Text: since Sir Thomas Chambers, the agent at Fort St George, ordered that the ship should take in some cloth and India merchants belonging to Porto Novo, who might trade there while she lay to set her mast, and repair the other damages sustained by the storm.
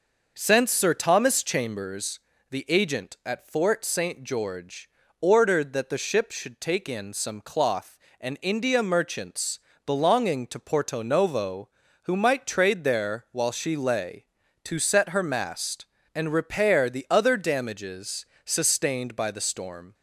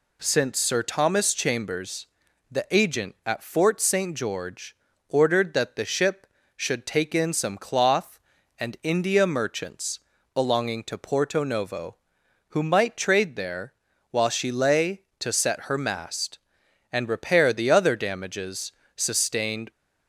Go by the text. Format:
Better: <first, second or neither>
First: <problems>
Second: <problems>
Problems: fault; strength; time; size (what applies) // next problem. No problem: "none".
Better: first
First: pauses between "merchants" and "belonging"; slight; at 9.5 s; 0.26 s long // pauses between "damages" and "sustained"; slight; at 18.2 s; 0.22 s long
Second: pauses between "merchants" and "belonging"; slight; at 9.9 s; 0.36 s long // pauses between "there" and "while"; at 13.7 s; 0.38 s long // pauses between "damages" and "sustained"; slight; at 18.7 s; 0.24 s long // stops before "by the storm"; at 19.7 s